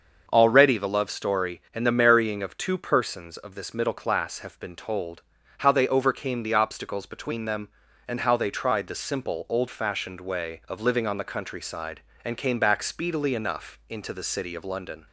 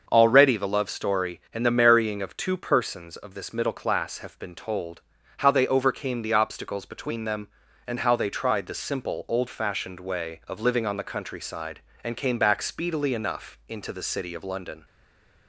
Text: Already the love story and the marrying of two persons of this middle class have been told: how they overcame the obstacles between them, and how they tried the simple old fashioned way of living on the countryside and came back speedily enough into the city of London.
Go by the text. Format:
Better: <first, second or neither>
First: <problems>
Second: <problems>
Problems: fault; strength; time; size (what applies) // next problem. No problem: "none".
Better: first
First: starts louder than the rest; until 1.3 s; 6.5 dB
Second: starts louder than the rest; until 1.1 s; 6.5 dB // stays silent after the last word; slight; from 14.8 s on; 0.6 s long